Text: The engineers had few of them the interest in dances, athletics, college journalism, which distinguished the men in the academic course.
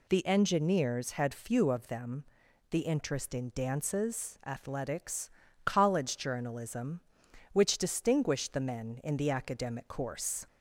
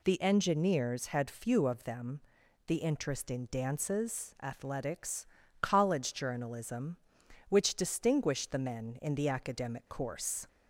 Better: neither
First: pauses between "them" and "the"; noticeable; at 2.2 s; 0.46 s long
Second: pauses between "them" and "the"; noticeable; at 2.2 s; 0.46 s long

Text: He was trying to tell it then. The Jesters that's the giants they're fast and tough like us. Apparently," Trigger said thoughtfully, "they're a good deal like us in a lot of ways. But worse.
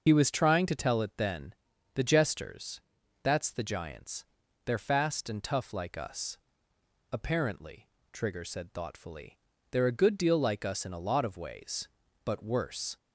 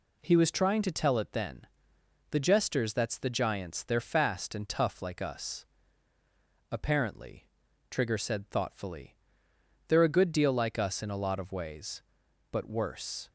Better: second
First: loses the start of "He"; at 0.0 s; 50 ms // pauses between "Jesters" and "that's"; at 2.7 s; 0.42 s long // pauses between "giants" and "they're"; at 4.2 s; 0.42 s long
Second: none

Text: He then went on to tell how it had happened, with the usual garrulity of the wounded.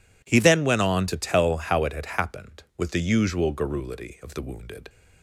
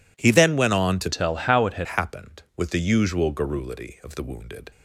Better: first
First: none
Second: changes voice from "tell" to "had"; from 1.1 to 1.8 s; 0.7 s long

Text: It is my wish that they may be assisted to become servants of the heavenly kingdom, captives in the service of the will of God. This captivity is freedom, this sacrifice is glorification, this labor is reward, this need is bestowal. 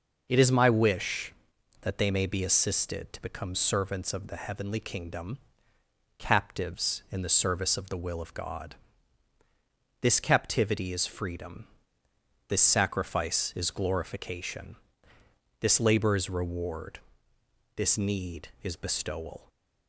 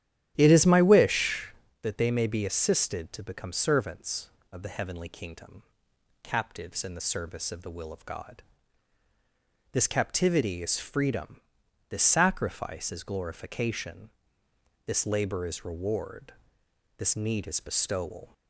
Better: first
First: none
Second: starts louder than the rest; strong; until 1.6 s; 11 dB

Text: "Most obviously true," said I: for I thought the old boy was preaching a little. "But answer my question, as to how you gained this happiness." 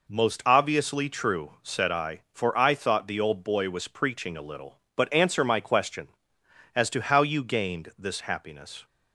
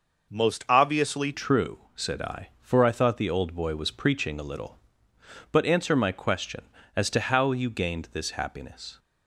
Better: first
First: none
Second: changes voice at "true"; from 1.3 s on; 7.6 s long

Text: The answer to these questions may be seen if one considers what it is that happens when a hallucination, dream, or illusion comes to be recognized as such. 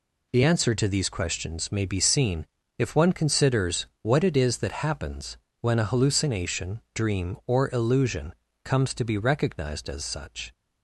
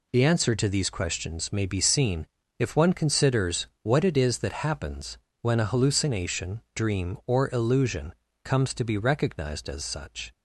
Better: neither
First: pauses between "seen" and "if"; slight; at 2.4 s; 0.34 s long // pauses between "considers" and "what"; slight; at 3.8 s; 0.16 s long // pauses between "happens" and "when"; slight; at 5.3 s; 0.24 s long // pauses between "illusion" and "comes"; slight; at 8.3 s; 0.28 s long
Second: pauses between "seen" and "if"; slight; at 2.2 s; 0.34 s long // pauses between "considers" and "what"; slight; at 3.6 s; 0.16 s long // pauses between "happens" and "when"; slight; at 5.1 s; 0.24 s long // pauses between "illusion" and "comes"; slight; at 8.1 s; 0.28 s long

